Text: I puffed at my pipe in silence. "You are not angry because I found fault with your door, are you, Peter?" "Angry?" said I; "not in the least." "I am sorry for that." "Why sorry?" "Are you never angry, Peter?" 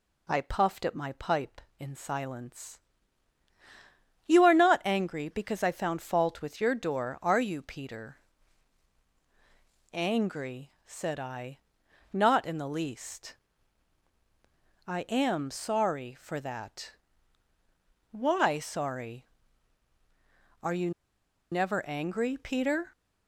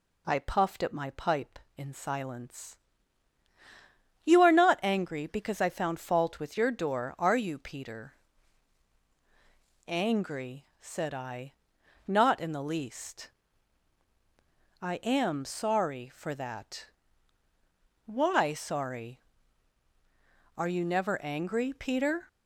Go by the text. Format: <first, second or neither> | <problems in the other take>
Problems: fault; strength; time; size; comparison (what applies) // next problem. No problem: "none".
second | pauses between "you" and "never"; noticeable; at 20.9 s; 0.60 s long